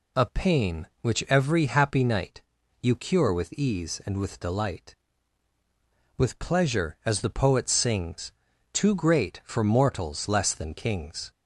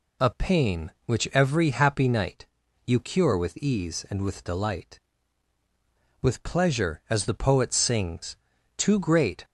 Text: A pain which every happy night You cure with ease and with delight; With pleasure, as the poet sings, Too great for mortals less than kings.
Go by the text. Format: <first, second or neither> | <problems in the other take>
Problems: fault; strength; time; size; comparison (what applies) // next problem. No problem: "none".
first | pauses between "night" and "You"; at 2.4 s; 0.40 s long; also in the first // stops before "for mortals less than kings"; at 9.4 s